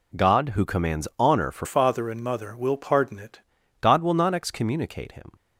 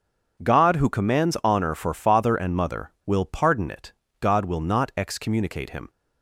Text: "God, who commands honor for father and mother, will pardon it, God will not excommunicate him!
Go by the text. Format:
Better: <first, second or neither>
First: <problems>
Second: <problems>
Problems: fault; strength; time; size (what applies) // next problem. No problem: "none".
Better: second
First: changes voice from "father" to "it"; from 1.6 to 3.3 s; 1.7 s long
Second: none